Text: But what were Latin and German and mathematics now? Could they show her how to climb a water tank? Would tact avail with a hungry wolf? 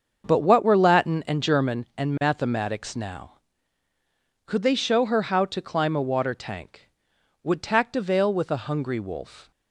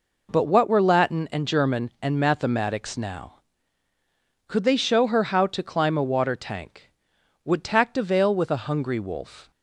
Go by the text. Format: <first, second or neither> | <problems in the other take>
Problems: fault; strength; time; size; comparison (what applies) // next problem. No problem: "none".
second | starts louder than the rest; until 1.7 s; 6.5 dB